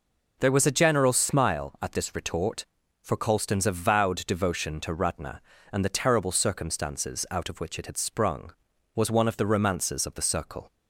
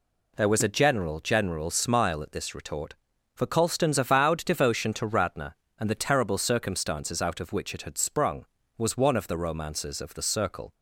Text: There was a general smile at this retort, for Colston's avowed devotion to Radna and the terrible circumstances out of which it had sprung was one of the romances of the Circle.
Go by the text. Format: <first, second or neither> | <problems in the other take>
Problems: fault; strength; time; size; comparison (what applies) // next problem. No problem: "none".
first | says "general" twice; at 1.1 s